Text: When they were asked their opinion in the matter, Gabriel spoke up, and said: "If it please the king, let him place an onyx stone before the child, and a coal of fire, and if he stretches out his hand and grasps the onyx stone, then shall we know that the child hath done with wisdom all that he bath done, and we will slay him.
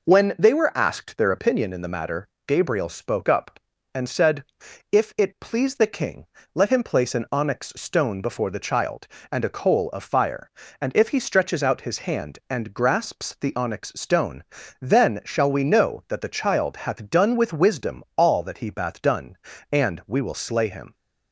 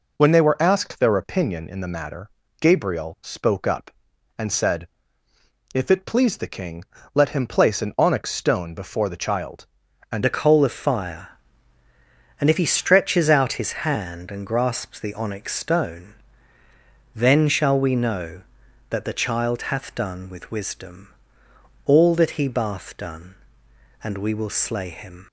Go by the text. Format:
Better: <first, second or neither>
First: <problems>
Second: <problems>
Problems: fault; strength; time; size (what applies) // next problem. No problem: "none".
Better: first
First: none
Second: changes voice at "a"; from 10.2 s on; 15.0 s long // pauses between "wisdom" and "all"; noticeable; at 21.0 s; 0.76 s long